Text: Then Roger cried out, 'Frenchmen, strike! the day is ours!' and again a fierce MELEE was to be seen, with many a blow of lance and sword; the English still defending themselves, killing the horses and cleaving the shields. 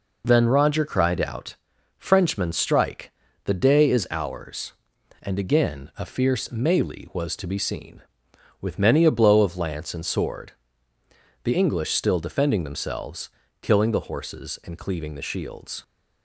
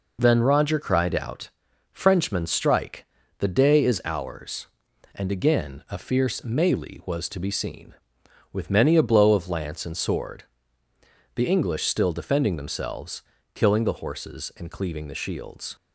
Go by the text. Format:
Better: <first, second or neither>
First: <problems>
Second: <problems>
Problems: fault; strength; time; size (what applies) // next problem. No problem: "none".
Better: neither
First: none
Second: none